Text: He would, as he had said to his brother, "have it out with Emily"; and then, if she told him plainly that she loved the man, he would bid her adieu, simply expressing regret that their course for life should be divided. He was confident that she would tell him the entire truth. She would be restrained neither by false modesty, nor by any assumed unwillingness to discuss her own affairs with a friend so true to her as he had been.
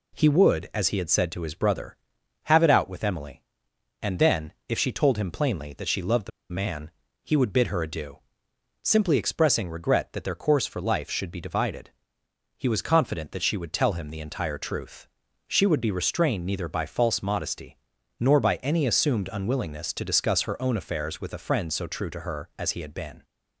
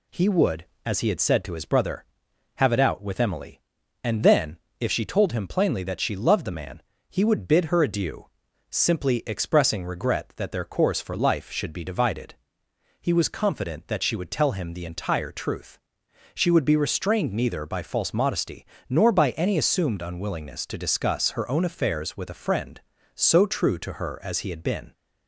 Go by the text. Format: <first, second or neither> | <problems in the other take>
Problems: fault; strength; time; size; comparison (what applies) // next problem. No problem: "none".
second | pauses between "the" and "man"; slight; at 6.3 s; 0.21 s long